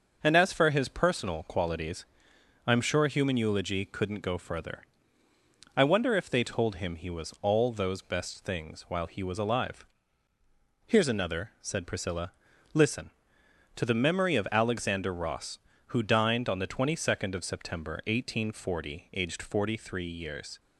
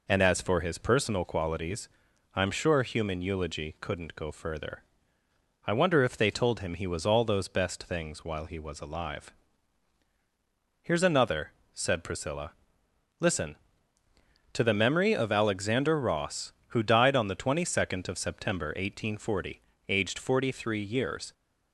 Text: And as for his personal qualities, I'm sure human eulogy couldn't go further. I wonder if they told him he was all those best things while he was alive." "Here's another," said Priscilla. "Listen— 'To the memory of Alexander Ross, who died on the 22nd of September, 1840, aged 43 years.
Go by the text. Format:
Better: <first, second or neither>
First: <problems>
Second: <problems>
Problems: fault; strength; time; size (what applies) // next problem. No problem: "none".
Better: second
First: starts louder than the rest; until 1.2 s; 6.5 dB // says "dined" for "died"; at 16.0 s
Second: none